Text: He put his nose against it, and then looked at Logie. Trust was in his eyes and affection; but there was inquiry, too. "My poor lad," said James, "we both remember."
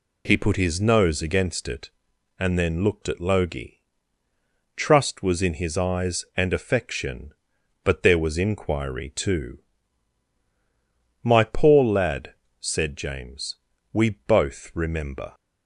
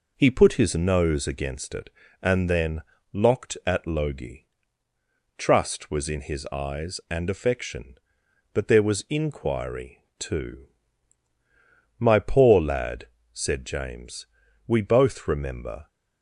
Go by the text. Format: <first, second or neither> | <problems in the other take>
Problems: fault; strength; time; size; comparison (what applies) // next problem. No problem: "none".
first | says "locked" for "looked"; at 3.1 s